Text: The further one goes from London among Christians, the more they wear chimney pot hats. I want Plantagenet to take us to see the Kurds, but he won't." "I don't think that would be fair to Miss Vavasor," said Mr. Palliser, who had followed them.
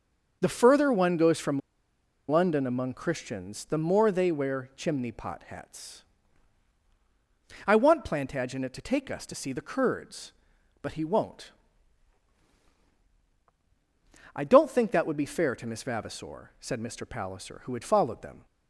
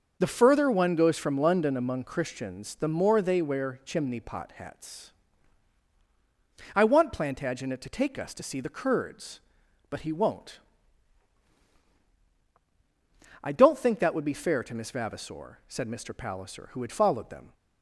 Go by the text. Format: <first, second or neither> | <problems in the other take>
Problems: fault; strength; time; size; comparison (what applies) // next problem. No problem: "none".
second | starts louder than the rest; noticeable; until 1.4 s; 6 dB; noticeable in the second // pauses between "from" and "London"; noticeable; at 1.6 s; 0.69 s long